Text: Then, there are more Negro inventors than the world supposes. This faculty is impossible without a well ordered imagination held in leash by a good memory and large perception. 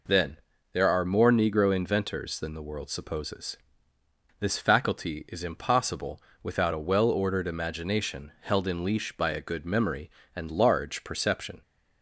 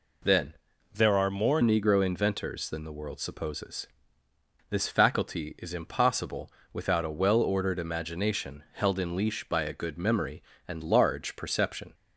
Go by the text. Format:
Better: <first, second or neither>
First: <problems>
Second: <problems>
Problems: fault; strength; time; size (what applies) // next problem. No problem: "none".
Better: first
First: pauses between "impossible" and "without"; slight; at 6.2 s; 0.22 s long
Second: changes voice from "there" to "more"; from 0.9 to 1.6 s; 0.7 s long // pauses between "impossible" and "without"; slight; at 6.5 s; 0.22 s long